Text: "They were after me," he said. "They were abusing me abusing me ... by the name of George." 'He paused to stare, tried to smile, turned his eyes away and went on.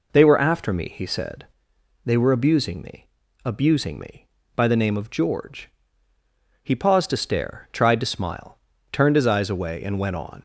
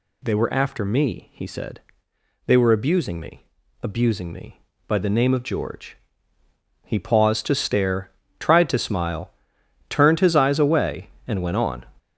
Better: first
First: pauses between "me" and "abusing"; at 3.0 s; 0.40 s long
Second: gets louder; strong; throughout; 8 dB // pauses between "me" and "abusing"; slight; at 3.4 s; 0.36 s long

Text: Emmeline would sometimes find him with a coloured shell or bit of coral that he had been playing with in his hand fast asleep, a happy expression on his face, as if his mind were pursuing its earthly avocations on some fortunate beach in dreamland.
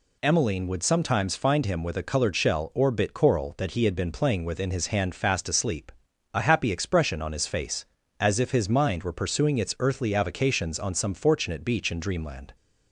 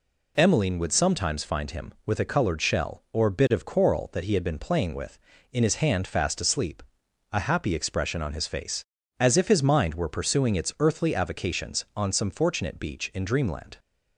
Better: second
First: skips "of"; at 3.1 s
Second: none

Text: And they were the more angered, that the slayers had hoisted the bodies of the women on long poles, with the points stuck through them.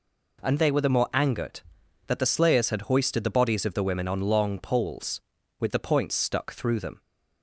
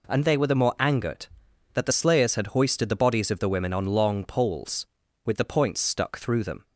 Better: neither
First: none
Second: none

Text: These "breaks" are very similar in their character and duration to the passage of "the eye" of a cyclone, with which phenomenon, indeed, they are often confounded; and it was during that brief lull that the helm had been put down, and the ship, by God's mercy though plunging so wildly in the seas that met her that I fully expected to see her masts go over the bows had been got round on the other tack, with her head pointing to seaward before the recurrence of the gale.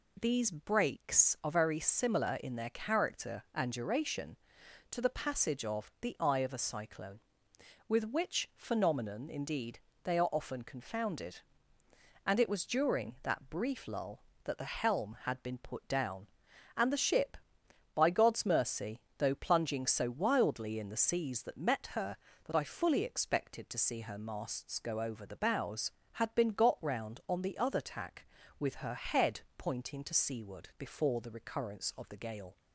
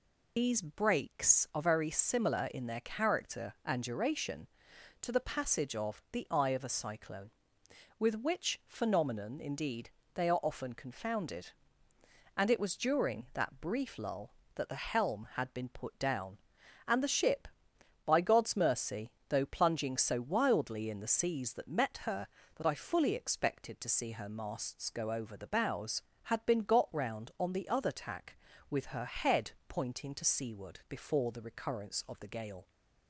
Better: first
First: pauses between "mercy" and "though"; slight; at 18.9 s; 0.18 s long // pauses between "head" and "pointing"; slight; at 29.3 s; 0.16 s long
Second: loses the start of "These"; at 0.3 s; 90 ms // pauses between "mercy" and "though"; slight; at 19.1 s; 0.18 s long // pauses between "head" and "pointing"; slight; at 29.5 s; 0.16 s long

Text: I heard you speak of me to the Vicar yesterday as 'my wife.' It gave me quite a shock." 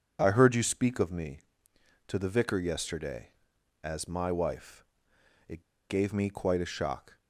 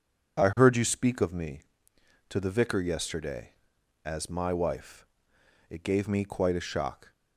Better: second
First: pauses between "It" and "gave"; slight; at 5.6 s; 0.27 s long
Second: none

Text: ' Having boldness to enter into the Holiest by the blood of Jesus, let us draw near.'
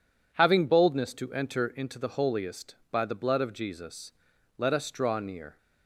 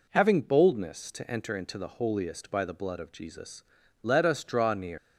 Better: first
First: none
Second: leaves "near" unfinished; at 4.9 s; 125 ms

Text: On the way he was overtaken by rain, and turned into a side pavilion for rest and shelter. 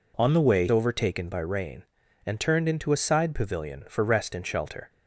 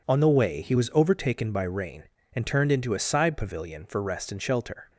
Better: second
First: skips "he was"; at 0.6 s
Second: none

